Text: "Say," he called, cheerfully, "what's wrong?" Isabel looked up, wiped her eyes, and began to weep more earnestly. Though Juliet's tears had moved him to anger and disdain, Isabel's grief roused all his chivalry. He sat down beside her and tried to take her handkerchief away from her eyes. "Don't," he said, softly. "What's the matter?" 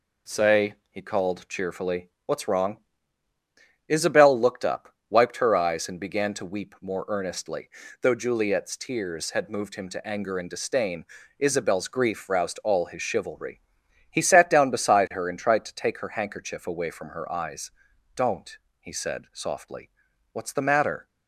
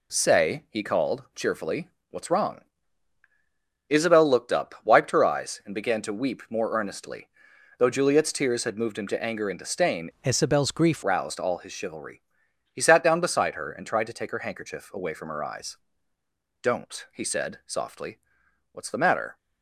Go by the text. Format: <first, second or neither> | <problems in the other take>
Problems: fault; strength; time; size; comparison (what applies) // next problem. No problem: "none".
first | changes voice from "Isabel's" to "grief"; from 10.2 to 11.0 s; 0.8 s long